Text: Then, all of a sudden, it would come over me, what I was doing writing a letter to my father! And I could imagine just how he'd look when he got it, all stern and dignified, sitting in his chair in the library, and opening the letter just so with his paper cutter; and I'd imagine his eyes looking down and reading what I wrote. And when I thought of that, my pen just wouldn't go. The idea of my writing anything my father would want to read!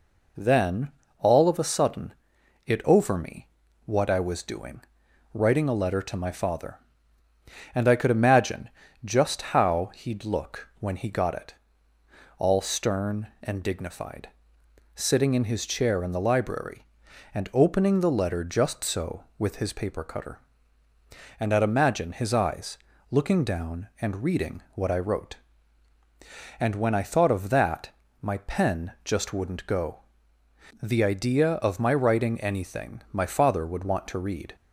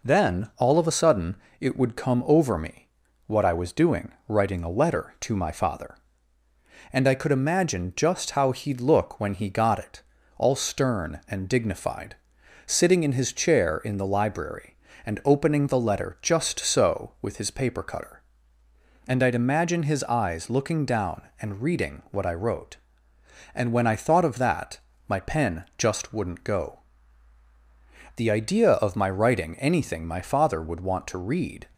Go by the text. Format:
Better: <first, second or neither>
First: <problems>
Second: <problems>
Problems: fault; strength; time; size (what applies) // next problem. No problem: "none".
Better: second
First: skips "would come"; at 2.8 s // pauses between "doing" and "writing"; noticeable; at 4.8 s; 0.52 s long // pauses between "imagine" and "just"; slight; at 8.6 s; 0.36 s long // pauses between "eyes" and "looking"; slight; at 22.7 s; 0.32 s long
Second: pauses between "doing" and "writing"; slight; at 4.1 s; 0.16 s long